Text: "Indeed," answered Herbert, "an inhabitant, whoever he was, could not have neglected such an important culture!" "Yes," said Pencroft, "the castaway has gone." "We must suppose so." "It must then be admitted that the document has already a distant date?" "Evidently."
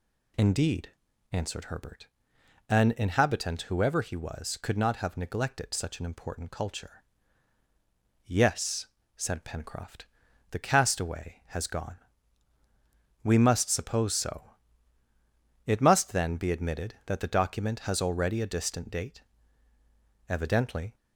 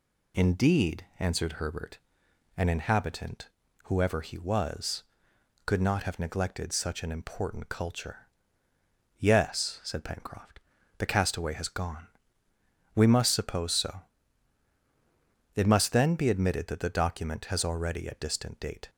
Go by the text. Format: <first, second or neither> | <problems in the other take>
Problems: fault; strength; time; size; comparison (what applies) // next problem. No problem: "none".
first | stops before "Evidently"; at 18.8 s